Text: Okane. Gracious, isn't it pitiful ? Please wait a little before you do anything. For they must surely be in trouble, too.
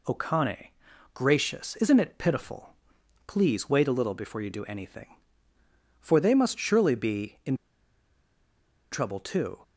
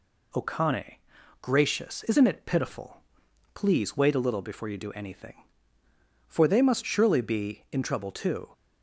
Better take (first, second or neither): second